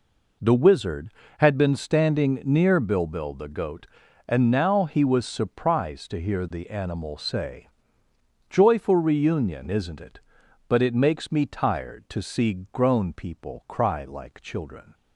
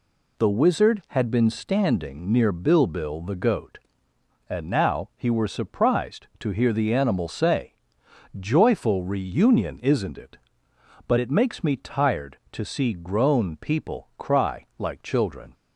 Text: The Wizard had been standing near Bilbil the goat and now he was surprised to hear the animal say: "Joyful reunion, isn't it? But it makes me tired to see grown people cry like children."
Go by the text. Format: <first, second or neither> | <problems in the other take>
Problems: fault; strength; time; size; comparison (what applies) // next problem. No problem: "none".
first | says "were" for "was"; at 5.2 s